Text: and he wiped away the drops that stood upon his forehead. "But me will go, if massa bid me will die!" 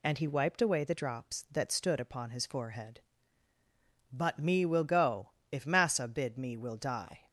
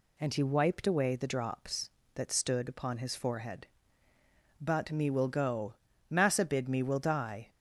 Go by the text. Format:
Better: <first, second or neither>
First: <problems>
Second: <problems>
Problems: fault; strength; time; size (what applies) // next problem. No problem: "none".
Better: first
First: none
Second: skips "if"; at 5.9 s